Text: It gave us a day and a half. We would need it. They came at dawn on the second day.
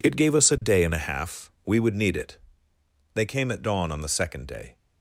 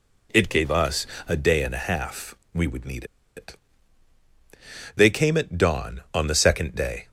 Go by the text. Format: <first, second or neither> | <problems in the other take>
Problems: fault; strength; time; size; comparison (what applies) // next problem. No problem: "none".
first | pauses between "us" and "a"; slight; at 1.0 s; 0.20 s long // pauses between "need" and "it"; slight; at 3.0 s; 0.32 s long